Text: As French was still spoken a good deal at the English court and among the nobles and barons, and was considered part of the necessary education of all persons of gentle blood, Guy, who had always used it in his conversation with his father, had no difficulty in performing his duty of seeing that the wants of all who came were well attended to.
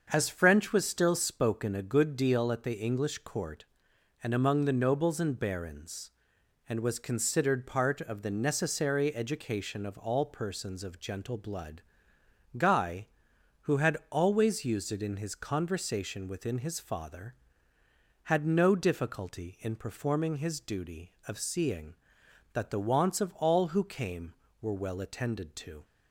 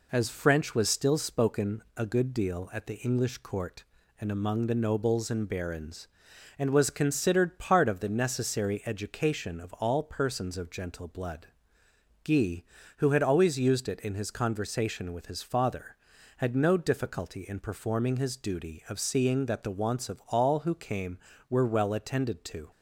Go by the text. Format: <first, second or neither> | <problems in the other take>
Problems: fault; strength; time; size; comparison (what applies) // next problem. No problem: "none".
second | starts louder than the rest; until 1.1 s; 6.5 dB // says "within" for "with"; at 16.2 s